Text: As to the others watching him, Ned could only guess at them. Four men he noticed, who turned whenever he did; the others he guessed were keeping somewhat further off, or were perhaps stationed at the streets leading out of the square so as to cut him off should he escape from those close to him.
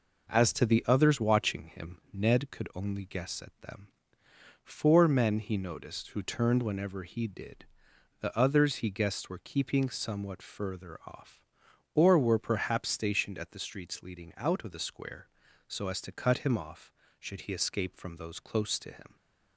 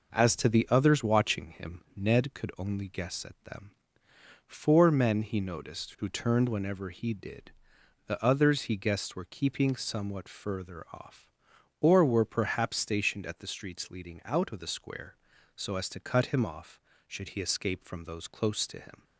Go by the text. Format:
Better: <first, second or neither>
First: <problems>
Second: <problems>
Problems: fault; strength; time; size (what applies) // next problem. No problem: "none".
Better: neither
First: none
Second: none